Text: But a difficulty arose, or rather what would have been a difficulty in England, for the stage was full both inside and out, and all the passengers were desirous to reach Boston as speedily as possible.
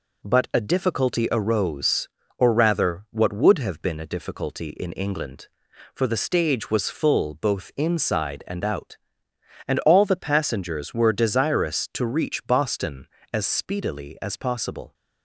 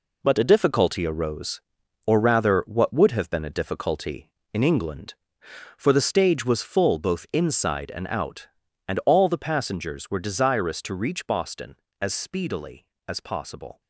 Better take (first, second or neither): first